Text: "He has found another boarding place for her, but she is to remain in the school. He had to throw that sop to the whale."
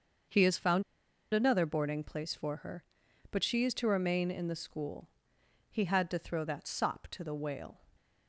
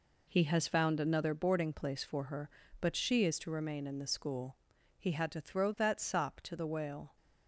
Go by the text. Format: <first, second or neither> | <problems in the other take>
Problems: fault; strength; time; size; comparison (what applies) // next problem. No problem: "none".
second | starts louder than the rest; until 1.8 s; 6.5 dB // pauses between "found" and "another"; noticeable; at 0.8 s; 0.50 s long